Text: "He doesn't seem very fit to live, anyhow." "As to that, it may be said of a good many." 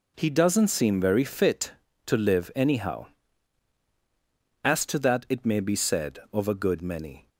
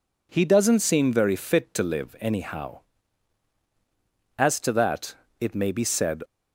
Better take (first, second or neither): first